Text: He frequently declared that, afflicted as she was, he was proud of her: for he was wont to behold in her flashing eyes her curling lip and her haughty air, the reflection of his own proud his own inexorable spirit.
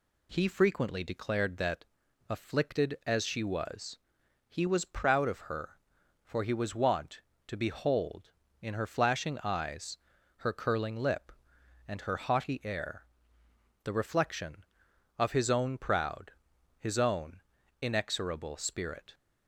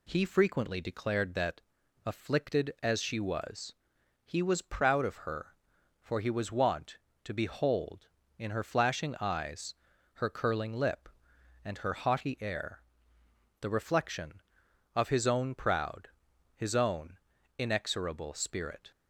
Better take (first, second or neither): neither